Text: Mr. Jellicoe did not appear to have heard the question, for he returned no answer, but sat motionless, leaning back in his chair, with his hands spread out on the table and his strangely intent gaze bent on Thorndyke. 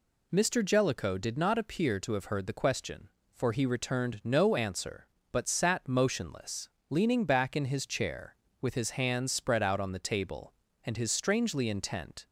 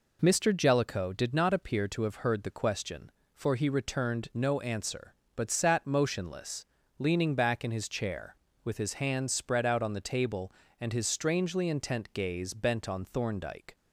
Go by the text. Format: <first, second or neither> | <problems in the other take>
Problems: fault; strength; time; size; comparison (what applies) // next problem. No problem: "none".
second | stops before "gaze bent on Thorndyke"; at 12.2 s